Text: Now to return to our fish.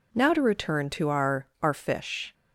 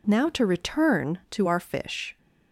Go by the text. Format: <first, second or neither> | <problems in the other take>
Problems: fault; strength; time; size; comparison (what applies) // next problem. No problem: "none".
second | says "our" twice; at 1.6 s